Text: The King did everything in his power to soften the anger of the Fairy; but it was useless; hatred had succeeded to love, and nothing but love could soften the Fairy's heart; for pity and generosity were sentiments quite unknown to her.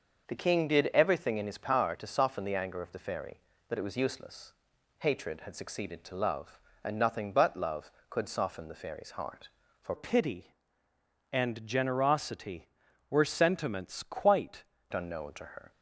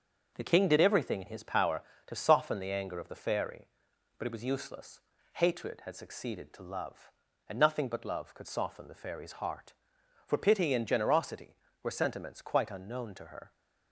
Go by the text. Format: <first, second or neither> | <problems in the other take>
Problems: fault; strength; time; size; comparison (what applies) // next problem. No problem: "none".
second | starts louder than the rest; until 1.3 s; 6 dB; also in the second // changes voice from "pity" to "quite"; from 9.9 to 14.6 s; 4.7 s long